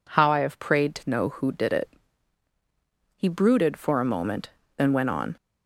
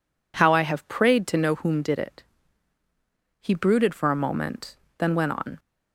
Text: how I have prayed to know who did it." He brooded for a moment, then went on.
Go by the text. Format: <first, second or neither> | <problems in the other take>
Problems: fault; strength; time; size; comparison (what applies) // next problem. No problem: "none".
first | says "whom" for "who"; at 1.5 s